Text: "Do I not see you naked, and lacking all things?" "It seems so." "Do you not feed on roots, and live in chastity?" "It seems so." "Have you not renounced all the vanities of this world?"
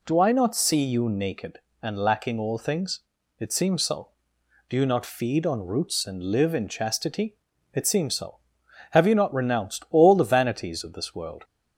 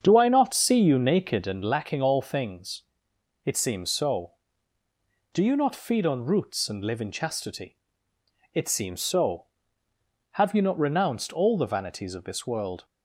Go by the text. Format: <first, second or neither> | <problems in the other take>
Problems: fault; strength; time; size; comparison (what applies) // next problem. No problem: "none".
first | starts louder than the rest; strong; until 1.8 s; 7.5 dB